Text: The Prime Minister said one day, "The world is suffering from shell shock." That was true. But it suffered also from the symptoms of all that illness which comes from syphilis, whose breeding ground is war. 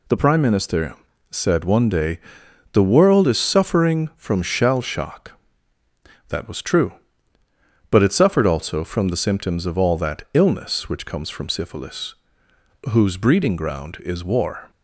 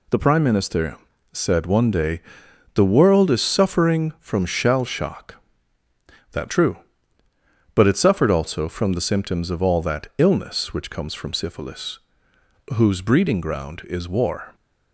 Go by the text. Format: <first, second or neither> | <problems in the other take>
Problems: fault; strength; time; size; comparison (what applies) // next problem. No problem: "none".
first | pauses between "Minister" and "said"; slight; at 0.9 s; 0.36 s long; slight in the first // skips "was"; at 6.4 s